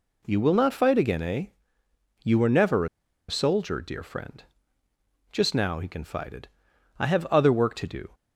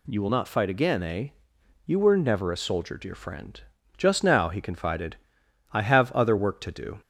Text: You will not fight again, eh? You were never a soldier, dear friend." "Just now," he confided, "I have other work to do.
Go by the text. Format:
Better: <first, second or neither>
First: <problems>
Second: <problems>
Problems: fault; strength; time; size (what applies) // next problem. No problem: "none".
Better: second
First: pauses between "never" and "a"; at 2.8 s; 0.42 s long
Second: none